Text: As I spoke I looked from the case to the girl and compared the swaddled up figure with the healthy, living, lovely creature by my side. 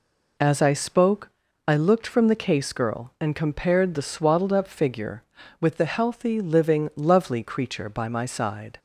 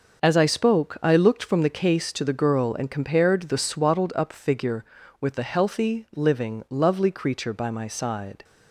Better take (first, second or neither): second